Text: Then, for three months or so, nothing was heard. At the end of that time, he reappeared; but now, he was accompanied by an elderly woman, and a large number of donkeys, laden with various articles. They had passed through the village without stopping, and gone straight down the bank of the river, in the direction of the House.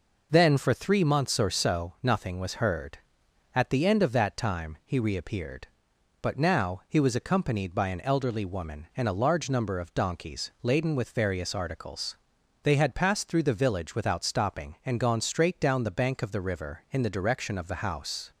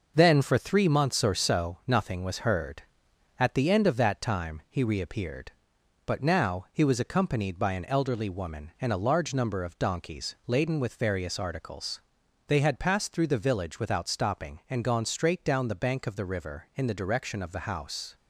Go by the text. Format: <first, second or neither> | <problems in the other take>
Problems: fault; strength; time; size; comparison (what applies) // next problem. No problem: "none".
first | gets quieter; noticeable; throughout; 5 dB